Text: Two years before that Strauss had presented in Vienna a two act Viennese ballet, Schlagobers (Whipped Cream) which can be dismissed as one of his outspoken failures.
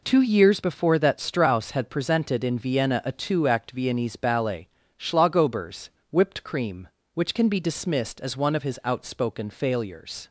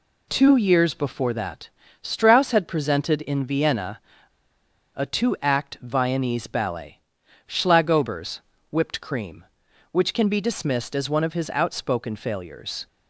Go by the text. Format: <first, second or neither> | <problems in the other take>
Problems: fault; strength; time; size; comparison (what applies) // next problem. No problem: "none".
first | pauses between "that" and "Strauss"; slight; at 1.6 s; 0.34 s long // pauses between "Vienna" and "a"; noticeable; at 3.9 s; 0.95 s long